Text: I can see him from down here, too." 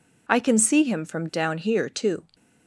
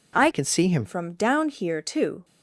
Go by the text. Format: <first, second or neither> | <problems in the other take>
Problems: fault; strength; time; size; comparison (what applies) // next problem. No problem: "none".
first | changes voice from "can" to "him"; from 0.3 to 0.8 s; 0.5 s long